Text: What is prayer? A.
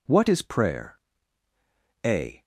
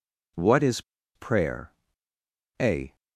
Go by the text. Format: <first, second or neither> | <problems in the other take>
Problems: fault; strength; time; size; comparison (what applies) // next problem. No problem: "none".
first | pauses between "is" and "prayer"; slight; at 0.8 s; 0.33 s long